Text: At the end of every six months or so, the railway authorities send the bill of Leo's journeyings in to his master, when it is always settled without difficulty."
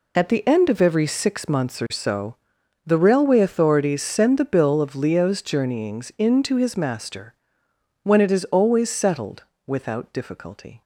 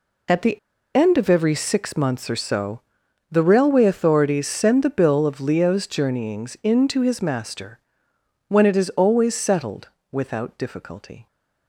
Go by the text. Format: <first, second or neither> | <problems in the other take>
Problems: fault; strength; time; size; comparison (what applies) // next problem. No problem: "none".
first | pauses between "the" and "end"; at 0.5 s; 0.38 s long // pauses between "settled" and "without"; slight; at 9.8 s; 0.22 s long; slight in the first